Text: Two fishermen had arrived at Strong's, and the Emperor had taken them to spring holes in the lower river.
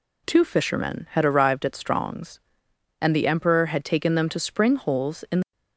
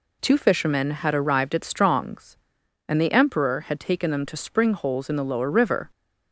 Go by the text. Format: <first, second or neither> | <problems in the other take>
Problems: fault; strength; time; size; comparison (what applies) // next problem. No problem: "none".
second | stops before "lower river"; at 5.5 s